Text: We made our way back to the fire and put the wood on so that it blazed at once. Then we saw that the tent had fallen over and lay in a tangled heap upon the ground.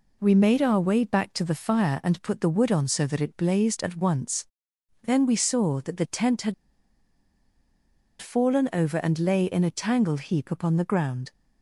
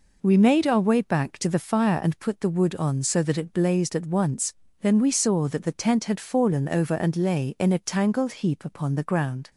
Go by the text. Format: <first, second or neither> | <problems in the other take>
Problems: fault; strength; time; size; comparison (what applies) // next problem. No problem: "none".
second | pauses between "had" and "fallen"; strong; at 6.5 s; 1.6 s long